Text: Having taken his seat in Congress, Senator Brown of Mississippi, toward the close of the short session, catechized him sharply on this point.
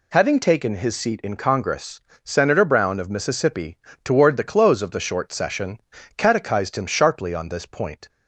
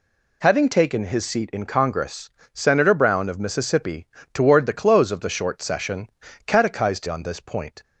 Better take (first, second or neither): first